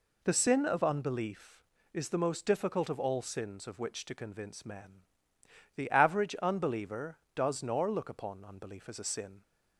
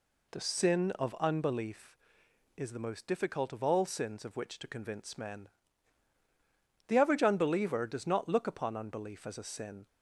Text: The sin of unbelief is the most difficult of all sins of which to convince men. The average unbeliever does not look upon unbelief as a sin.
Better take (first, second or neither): second